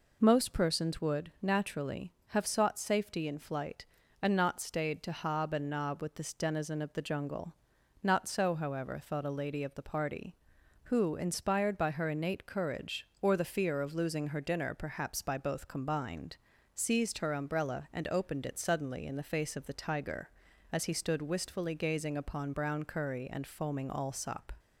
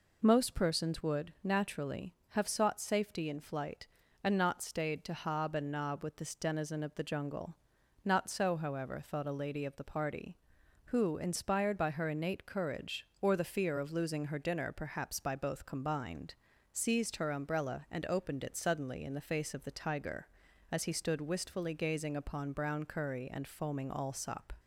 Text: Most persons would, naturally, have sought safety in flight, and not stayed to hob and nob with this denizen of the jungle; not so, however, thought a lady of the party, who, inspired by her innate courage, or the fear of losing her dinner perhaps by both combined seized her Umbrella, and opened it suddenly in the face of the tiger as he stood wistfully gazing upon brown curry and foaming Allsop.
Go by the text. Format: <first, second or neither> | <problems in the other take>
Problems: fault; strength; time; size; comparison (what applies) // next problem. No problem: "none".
neither | pauses between "combined" and "seized"; the same in both